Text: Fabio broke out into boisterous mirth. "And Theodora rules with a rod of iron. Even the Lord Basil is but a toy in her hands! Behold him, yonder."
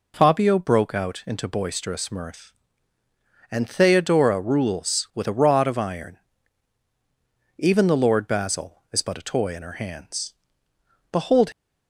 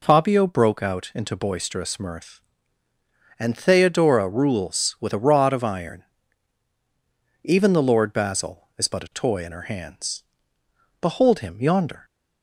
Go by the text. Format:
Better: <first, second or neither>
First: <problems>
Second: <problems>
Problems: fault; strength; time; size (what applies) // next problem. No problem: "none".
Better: second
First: stops before "him yonder"; at 11.5 s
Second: none